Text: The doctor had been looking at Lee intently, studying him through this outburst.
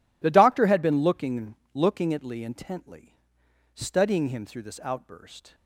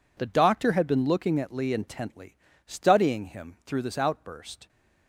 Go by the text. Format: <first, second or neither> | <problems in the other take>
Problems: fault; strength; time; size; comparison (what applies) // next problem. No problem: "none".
second | says "looking" twice; at 1.7 s